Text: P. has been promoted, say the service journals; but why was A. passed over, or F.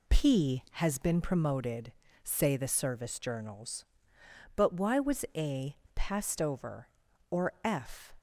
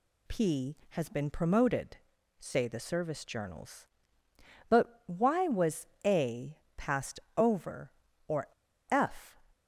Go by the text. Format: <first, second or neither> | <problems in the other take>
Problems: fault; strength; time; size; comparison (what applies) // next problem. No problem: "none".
first | pauses between "was" and "A"; slight; at 5.8 s; 0.18 s long // pauses between "passed" and "over"; slight; at 7.2 s; 0.16 s long // pauses between "or" and "F"; at 8.4 s; 0.44 s long